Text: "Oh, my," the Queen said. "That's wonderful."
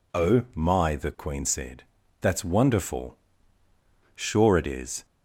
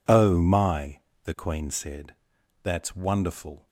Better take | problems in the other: second | goes on to say "Sure it is"; noticeable; from 4.1 s on; 0.90 s long

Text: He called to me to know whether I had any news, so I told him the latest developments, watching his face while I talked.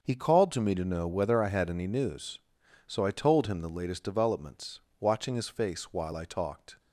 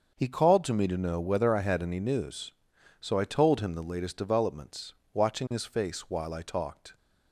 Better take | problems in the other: neither | starts louder than the rest; the same in both

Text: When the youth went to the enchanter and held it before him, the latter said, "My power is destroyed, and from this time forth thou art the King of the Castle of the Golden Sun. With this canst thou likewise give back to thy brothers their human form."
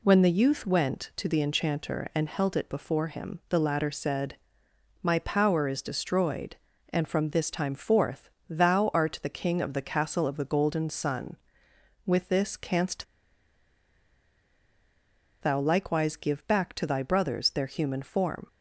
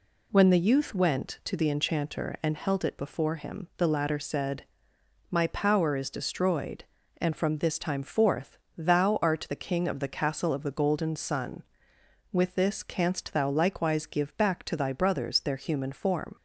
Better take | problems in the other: second | pauses between "forth" and "thou"; slight; at 8.2 s; 0.20 s long; slight in the second // pauses between "canst" and "thou"; strong; at 13.0 s; 2.3 s long

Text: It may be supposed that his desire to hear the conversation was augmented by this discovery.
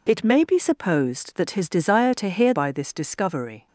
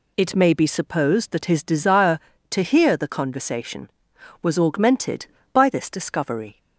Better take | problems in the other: second | skips "the conversation was augmented"; at 2.5 s

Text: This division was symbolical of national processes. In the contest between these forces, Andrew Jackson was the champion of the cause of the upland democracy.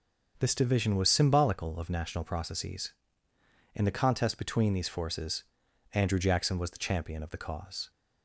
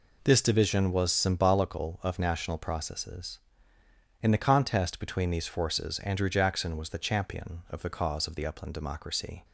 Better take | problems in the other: second | starts louder than the rest; until 1.4 s; 6 dB // stops before "of the upland democracy"; at 7.8 s

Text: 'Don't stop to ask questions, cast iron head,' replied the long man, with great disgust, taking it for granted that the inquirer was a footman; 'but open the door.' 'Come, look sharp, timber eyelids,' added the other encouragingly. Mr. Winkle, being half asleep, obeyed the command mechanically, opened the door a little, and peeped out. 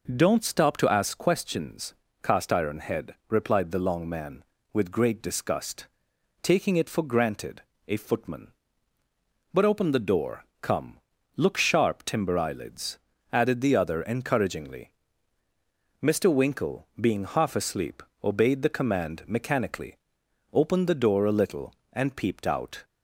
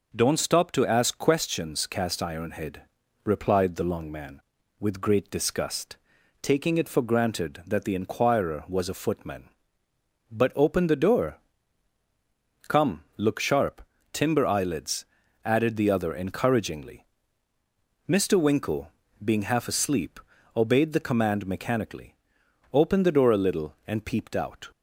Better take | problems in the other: second | skips "that the inquirer was"; at 7.7 s

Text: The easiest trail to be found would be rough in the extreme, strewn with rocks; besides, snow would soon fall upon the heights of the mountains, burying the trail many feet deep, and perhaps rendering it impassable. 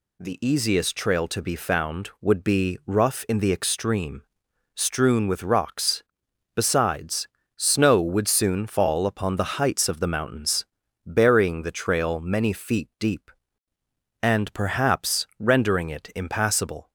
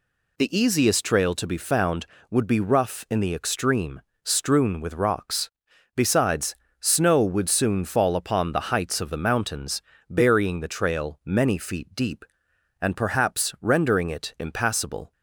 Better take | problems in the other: neither | none

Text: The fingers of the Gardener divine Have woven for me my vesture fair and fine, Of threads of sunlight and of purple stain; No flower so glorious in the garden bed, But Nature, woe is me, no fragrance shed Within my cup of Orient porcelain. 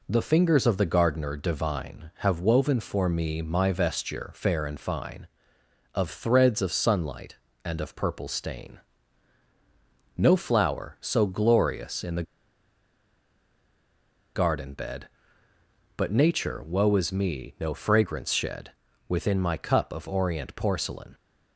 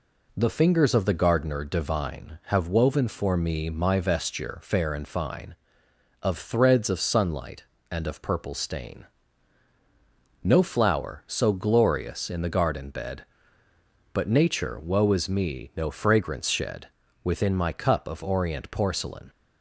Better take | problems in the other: second | pauses between "the" and "garden"; strong; at 12.2 s; 2.1 s long // pauses between "shed" and "Within"; slight; at 18.7 s; 0.36 s long; slight in the second

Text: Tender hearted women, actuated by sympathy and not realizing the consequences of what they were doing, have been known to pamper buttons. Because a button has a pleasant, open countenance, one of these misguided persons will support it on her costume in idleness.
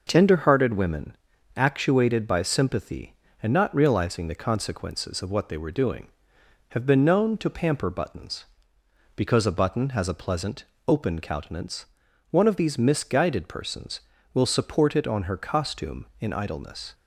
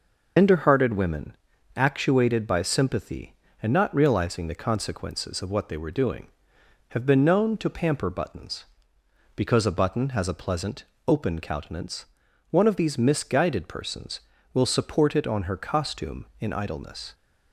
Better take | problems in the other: first | loses the start of "Tender"; at 0.3 s; 95 ms

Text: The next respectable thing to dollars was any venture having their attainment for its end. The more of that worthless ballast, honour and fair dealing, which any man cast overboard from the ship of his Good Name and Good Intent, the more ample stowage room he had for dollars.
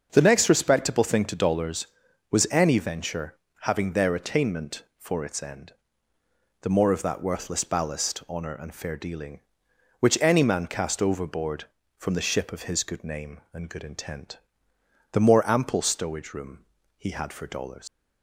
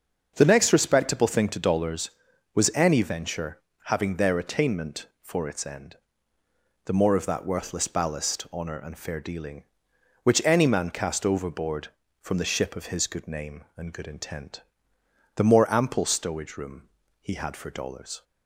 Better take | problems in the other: second | starts louder than the rest; until 1.1 s; 6.5 dB; also in the second // pauses between "venture" and "having"; slight; at 3.3 s; 0.26 s long; slight in the second // pauses between "room" and "he"; slight; at 16.6 s; 0.34 s long; slight in the second // leaves "dollars" unfinished; at 17.8 s; 120 ms

